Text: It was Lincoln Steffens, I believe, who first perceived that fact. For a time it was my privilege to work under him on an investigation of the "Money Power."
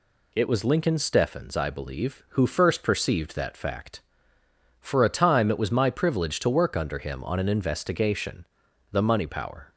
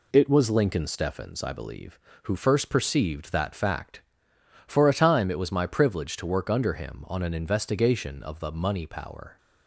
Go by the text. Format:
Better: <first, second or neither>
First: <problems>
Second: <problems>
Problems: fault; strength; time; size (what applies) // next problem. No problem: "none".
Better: second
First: skips "of"; at 8.6 s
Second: none